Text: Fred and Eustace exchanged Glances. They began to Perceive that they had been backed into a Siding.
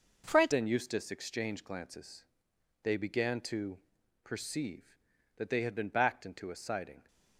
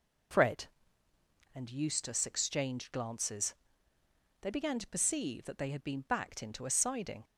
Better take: second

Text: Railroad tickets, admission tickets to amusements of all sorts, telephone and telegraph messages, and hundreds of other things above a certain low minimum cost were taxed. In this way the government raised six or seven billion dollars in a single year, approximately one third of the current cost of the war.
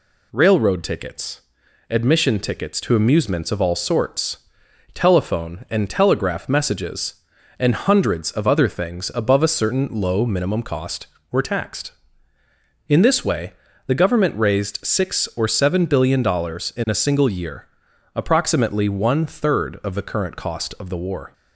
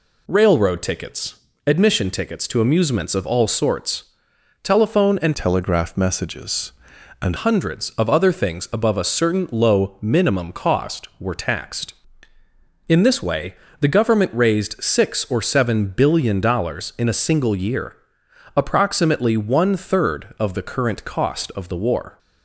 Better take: first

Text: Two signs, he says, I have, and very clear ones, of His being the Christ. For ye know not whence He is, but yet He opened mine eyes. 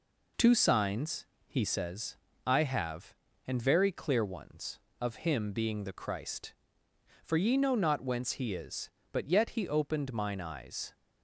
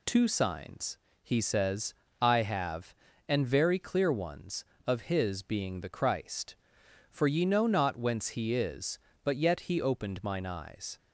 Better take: second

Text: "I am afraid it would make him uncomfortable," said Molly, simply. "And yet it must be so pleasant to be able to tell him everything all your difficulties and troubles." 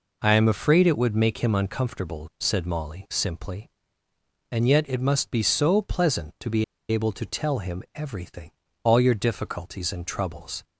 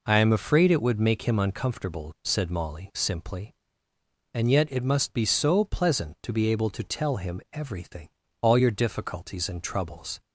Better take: second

